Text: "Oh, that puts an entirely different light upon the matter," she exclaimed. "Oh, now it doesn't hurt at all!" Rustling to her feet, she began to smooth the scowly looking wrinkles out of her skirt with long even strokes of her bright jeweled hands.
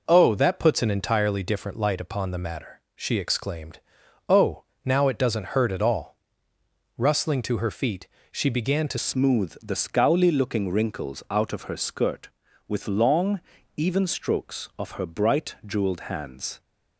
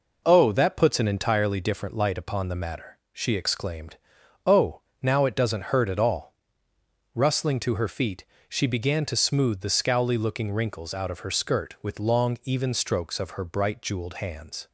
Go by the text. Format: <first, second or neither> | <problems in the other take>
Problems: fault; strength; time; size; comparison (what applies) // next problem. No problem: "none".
second | changes voice at "smooth"; from 8.9 s on; 7.6 s long // pauses between "long" and "even"; slight; at 13.3 s; 0.36 s long